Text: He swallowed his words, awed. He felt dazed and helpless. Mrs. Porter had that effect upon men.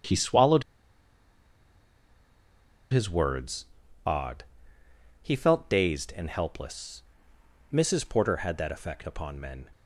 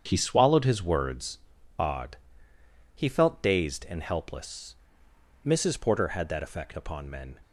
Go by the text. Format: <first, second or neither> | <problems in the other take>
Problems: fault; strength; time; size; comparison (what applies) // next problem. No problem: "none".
second | starts louder than the rest; strong; until 3.3 s; 8 dB; strong in the second // pauses between "swallowed" and "his"; strong; at 0.6 s; 2.2 s long